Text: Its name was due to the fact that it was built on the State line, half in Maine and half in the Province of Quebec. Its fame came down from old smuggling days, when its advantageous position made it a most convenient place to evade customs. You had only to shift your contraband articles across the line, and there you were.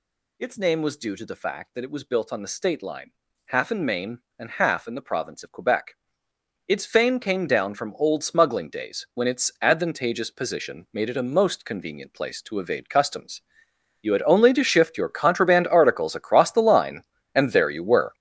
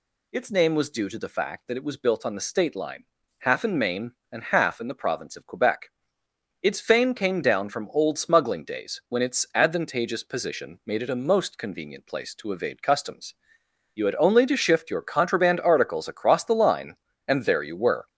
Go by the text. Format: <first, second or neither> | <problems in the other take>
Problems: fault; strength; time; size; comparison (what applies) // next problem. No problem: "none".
second | gets louder; strong; throughout; 10.5 dB